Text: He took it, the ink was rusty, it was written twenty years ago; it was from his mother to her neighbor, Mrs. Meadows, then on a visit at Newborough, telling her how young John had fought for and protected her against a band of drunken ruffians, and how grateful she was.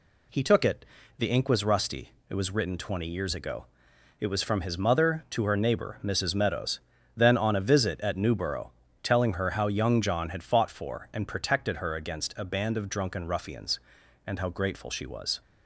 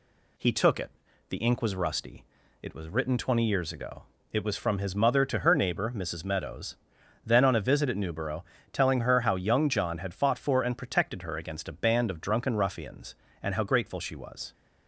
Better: neither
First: none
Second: none

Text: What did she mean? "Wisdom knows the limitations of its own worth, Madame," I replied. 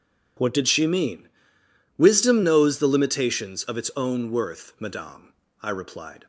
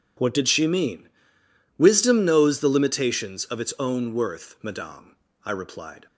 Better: neither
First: none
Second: none

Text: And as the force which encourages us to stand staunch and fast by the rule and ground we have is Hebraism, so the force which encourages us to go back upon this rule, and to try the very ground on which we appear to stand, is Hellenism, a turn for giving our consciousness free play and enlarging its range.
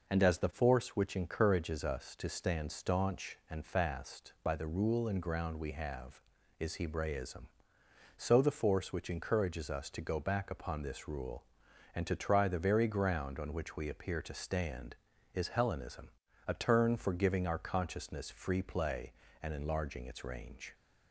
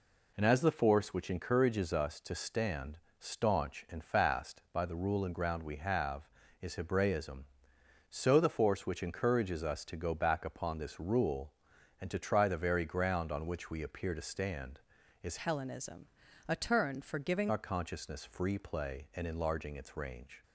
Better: first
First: none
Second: pauses between "stand" and "staunch"; slight; at 2.9 s; 0.20 s long // changes voice from "Hellenism" to "giving"; from 15.3 to 17.5 s; 2.2 s long

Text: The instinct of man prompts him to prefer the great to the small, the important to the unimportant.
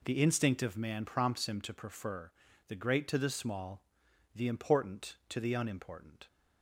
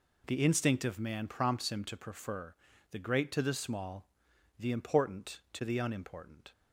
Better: neither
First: pauses between "prefer" and "the"; slight; at 2.3 s; 0.36 s long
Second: pauses between "prefer" and "the"; slight; at 2.5 s; 0.36 s long

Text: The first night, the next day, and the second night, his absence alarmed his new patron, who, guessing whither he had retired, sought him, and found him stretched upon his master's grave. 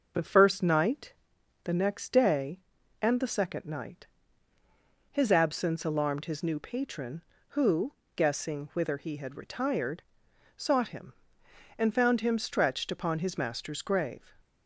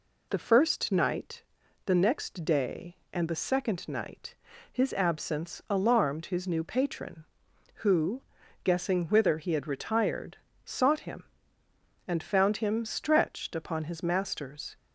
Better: first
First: none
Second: stops before "grave"; at 14.7 s

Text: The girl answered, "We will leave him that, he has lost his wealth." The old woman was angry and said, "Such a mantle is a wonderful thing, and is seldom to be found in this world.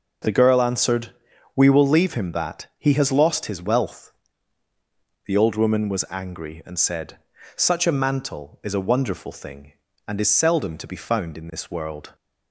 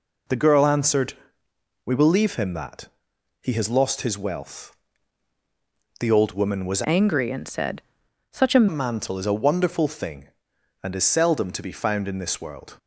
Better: first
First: none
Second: changes voice from "angry" to "a"; from 6.8 to 8.6 s; 1.8 s long

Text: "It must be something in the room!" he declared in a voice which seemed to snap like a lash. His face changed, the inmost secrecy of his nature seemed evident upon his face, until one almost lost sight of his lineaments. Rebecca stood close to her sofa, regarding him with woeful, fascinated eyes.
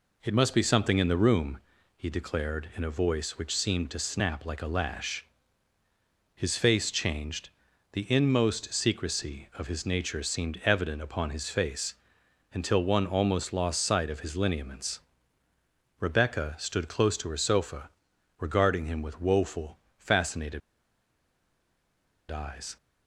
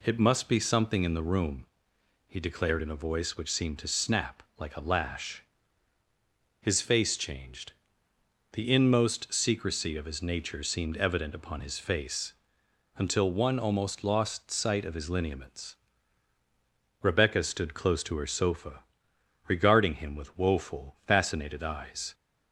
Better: second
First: pauses between "fascinated" and "eyes"; strong; at 20.6 s; 1.7 s long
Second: none

